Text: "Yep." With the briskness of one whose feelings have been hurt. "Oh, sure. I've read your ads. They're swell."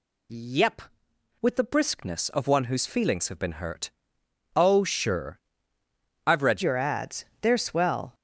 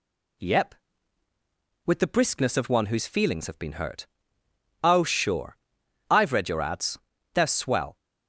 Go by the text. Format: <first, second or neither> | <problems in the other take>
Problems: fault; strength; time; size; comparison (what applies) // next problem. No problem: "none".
second | changes voice at "your"; from 6.6 s on; 1.5 s long